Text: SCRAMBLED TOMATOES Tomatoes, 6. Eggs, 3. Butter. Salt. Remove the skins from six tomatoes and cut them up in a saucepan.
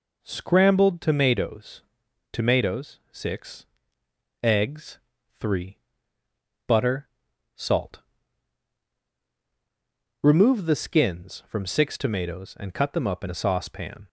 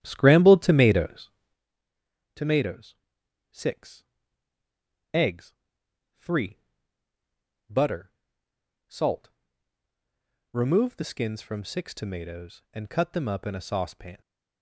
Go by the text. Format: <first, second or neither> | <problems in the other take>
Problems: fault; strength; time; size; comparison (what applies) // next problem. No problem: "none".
first | starts louder than the rest; strong; until 1.6 s; 11 dB // pauses between "TOMATOES" and "Tomatoes"; at 1.2 s; 1.0 s long; noticeable in the first